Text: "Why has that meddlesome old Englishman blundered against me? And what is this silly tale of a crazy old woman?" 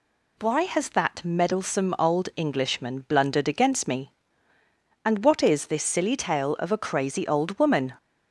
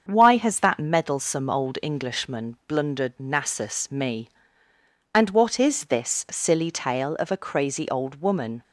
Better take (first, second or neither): first